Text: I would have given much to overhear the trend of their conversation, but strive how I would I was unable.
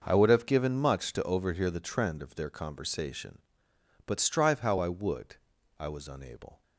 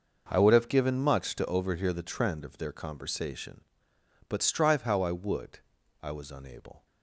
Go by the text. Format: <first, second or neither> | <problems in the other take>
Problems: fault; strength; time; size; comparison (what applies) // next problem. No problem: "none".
neither | pauses between "would" and "I"; the same in both